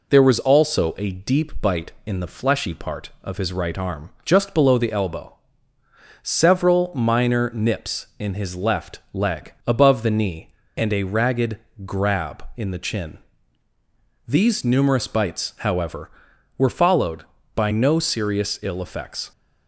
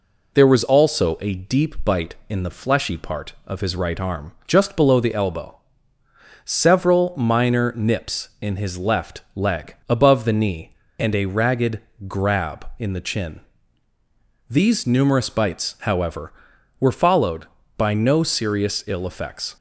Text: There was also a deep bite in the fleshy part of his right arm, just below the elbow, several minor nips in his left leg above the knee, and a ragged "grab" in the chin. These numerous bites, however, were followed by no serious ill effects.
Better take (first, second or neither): neither